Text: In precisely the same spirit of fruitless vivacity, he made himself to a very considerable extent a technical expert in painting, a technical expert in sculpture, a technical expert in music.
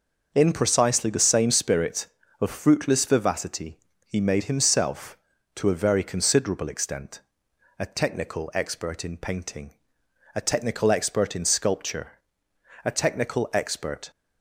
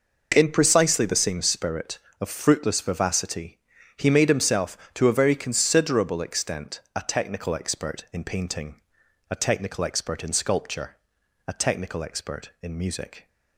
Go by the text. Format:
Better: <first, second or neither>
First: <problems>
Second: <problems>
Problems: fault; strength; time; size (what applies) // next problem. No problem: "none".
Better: second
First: pauses between "extent" and "a"; noticeable; at 7.2 s; 0.60 s long // stops before "in music"; at 14.1 s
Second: none